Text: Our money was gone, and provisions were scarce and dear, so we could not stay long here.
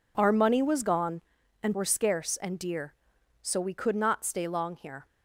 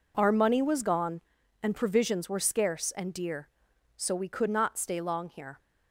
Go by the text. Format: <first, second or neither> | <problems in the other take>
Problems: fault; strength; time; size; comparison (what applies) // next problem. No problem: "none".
second | skips "provisions"; at 1.7 s